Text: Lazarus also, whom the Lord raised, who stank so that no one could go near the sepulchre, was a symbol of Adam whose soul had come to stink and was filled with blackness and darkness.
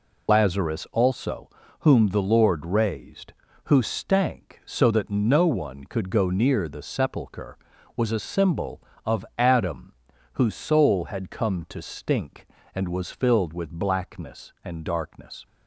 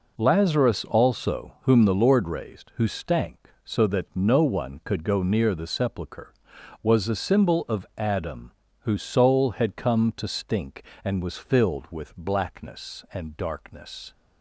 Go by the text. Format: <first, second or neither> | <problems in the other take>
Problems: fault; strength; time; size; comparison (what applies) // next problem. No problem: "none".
second | loses the start of "Lazarus"; at 0.2 s; 60 ms // pauses between "Adam" and "whose"; at 9.9 s; 0.40 s long; slight in the second